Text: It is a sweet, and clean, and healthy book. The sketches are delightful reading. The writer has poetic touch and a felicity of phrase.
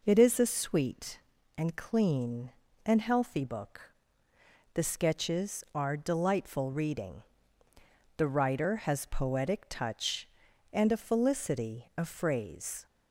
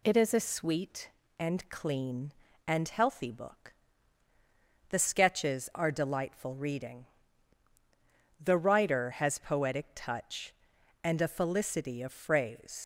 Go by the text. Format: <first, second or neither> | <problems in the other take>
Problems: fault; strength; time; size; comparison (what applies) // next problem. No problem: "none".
first | leaves "phrase" unfinished; at 12.8 s; 90 ms